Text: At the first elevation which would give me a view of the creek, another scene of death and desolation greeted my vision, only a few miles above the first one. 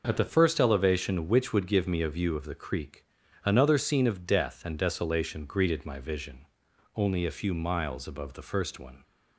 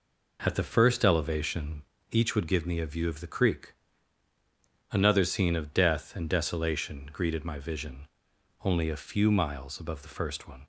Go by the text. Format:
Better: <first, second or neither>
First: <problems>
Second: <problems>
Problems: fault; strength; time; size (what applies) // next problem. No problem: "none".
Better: first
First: none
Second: says "each" for "which"; at 2.1 s